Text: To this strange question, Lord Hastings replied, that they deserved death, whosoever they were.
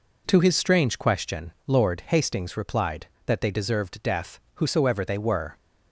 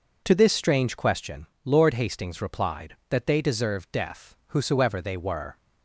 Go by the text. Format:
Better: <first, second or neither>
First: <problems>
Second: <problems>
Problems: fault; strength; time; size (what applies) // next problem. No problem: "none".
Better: second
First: says "his" for "this"; at 0.3 s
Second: none